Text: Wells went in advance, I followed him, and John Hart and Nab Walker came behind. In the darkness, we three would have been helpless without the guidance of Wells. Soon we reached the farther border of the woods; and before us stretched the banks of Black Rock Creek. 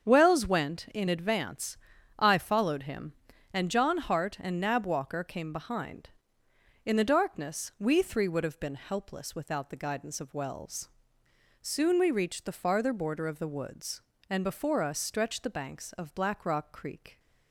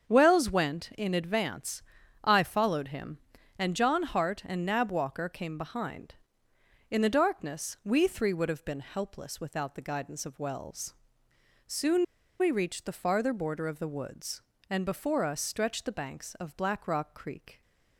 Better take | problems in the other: first | starts louder than the rest; until 1.1 s; 7 dB; strong in the first // pauses between "Soon" and "we"; slight; at 12.0 s; 0.35 s long

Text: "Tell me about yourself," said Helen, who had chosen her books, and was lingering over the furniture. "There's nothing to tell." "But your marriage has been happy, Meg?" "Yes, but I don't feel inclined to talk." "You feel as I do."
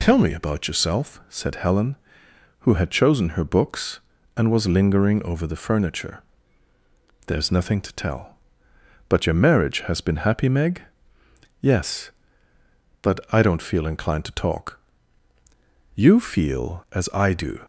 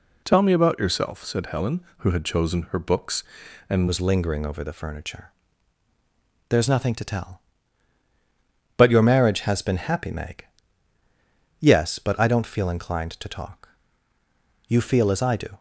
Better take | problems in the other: first | changes voice at "was"; from 3.8 s on; 11.7 s long

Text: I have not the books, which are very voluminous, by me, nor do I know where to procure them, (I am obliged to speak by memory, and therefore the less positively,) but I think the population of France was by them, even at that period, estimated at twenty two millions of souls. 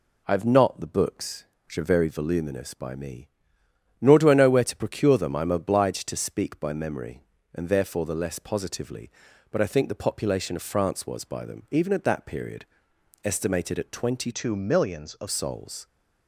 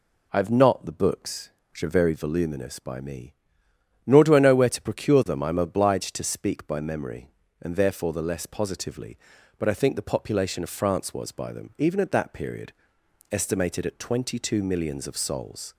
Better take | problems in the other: second | changes voice from "two" to "of"; from 14.3 to 15.2 s; 0.9 s long

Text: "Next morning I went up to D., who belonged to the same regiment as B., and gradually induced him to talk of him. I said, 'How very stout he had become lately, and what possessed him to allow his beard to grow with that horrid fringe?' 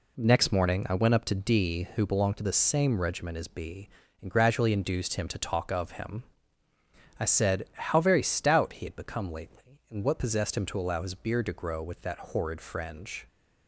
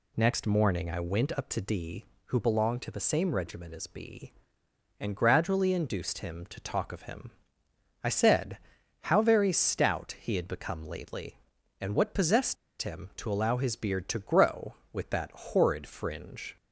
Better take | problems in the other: first | pauses between "possessed" and "him"; slight; at 12.5 s; 0.26 s long

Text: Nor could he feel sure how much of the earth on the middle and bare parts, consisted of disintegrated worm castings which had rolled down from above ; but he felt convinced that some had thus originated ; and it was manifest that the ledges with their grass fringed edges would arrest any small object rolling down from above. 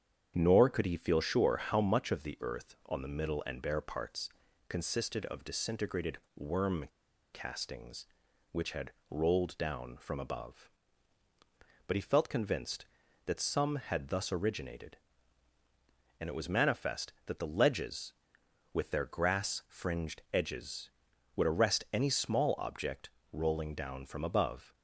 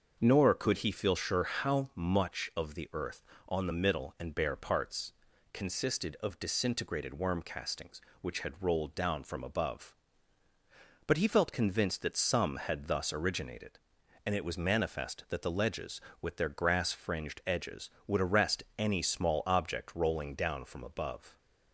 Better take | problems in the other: second | starts louder than the rest; strong; until 1.3 s; 8 dB; also in the second // pauses between "disintegrated" and "worm"; slight; at 6.1 s; 0.18 s long // pauses between "worm" and "castings"; noticeable; at 6.8 s; 0.48 s long // pauses between "had" and "rolled"; slight; at 8.9 s; 0.18 s long // pauses between "object" and "rolling"; slight; at 23.0 s; 0.22 s long

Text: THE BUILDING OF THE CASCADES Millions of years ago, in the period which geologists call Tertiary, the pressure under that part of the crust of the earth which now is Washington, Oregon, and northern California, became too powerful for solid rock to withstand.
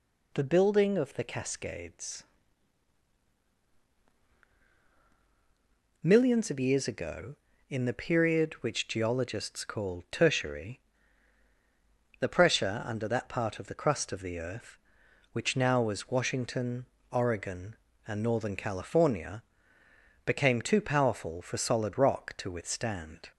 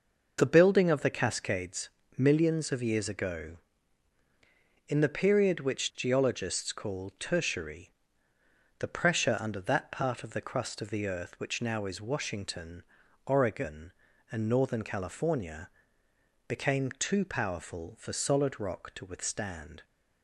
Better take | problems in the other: second | pauses between "CASCADES" and "Millions"; strong; at 2.2 s; 3.7 s long; slight in the second // says "was" for "is"; at 15.8 s

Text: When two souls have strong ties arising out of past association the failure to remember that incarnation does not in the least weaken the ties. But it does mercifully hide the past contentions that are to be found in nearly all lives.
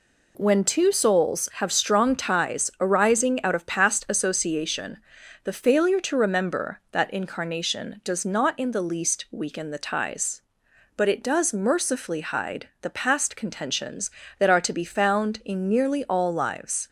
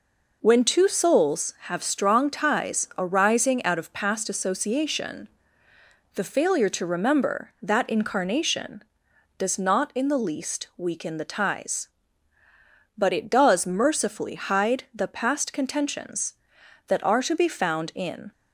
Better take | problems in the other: first | pauses between "association" and "the"; noticeable; at 5.2 s; 0.86 s long; noticeable in the first // stops before "nearly all lives"; at 18.3 s

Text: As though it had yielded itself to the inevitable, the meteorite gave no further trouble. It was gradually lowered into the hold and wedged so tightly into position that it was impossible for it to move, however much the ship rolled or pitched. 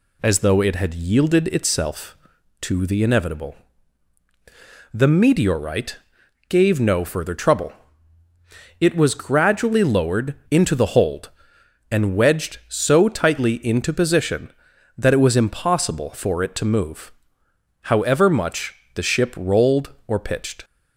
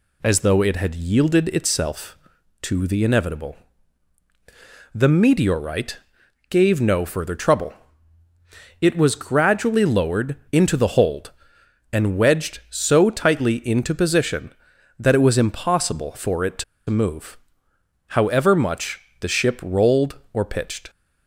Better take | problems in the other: first | pauses between "meteorite" and "gave"; noticeable; at 5.9 s; 0.54 s long; noticeable in the first // pauses between "lowered" and "into"; slight; at 10.3 s; 0.16 s long; slight in the first // pauses between "to" and "move"; slight; at 16.6 s; 0.25 s long // pauses between "much" and "the"; slight; at 18.9 s; 0.22 s long; slight in the first

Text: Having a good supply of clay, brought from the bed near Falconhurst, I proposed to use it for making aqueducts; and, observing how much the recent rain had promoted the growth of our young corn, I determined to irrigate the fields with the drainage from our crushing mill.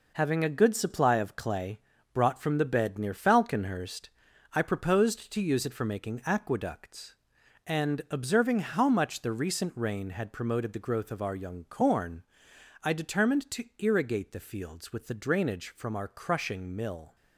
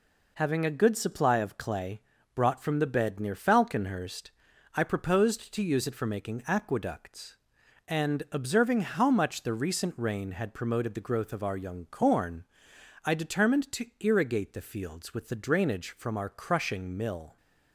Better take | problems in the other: second | gets quieter; throughout; 7 dB

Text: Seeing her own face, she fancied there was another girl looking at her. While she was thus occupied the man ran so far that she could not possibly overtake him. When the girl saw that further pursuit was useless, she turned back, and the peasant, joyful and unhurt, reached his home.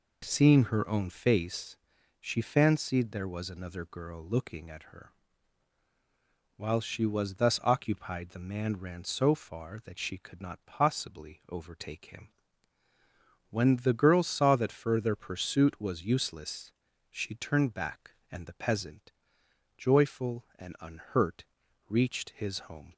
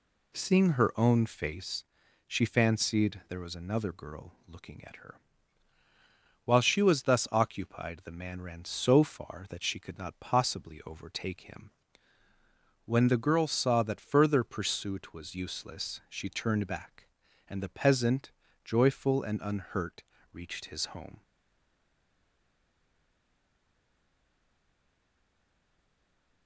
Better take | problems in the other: first | stays silent after the last word; strong; from 21.2 s on; 5.2 s long

